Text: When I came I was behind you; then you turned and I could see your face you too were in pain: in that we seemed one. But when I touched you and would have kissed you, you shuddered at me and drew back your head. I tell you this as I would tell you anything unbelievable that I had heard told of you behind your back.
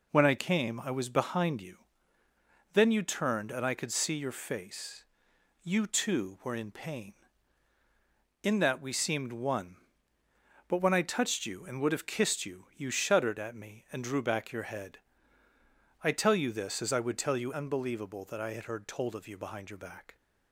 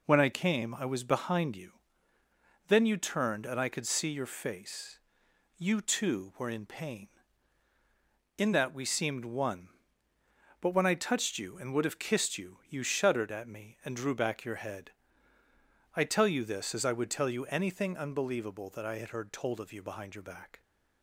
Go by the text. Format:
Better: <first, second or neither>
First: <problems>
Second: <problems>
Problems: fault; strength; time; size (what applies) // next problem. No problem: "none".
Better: second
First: pauses between "face" and "you"; noticeable; at 5.0 s; 0.56 s long // skips "anything"; at 17.5 s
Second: pauses between "face" and "you"; noticeable; at 4.9 s; 0.56 s long